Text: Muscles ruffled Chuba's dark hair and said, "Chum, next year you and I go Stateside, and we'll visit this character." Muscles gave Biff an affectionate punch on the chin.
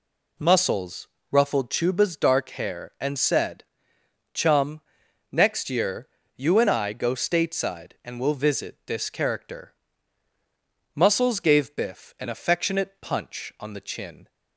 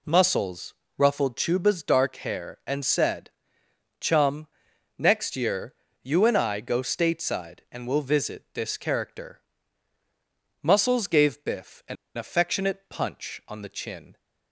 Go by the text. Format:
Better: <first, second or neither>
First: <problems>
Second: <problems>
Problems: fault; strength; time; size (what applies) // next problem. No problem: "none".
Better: first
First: pauses between "Muscles" and "ruffled"; slight; at 1.0 s; 0.24 s long // pauses between "year" and "you"; slight; at 6.0 s; 0.30 s long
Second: pauses between "Muscles" and "ruffled"; slight; at 0.7 s; 0.24 s long // pauses between "year" and "you"; slight; at 5.7 s; 0.30 s long // pauses between "an" and "affectionate"; slight; at 11.9 s; 0.20 s long